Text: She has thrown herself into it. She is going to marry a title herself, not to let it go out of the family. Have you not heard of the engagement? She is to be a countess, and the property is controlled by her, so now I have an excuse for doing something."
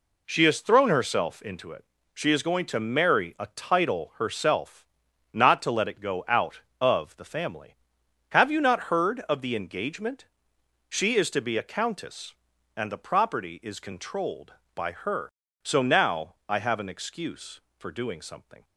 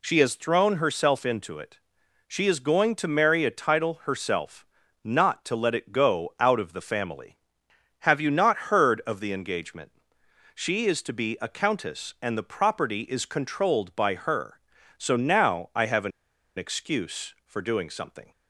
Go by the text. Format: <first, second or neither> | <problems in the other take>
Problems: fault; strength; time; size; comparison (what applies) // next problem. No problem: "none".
first | pauses between "an" and "excuse"; noticeable; at 16.1 s; 0.48 s long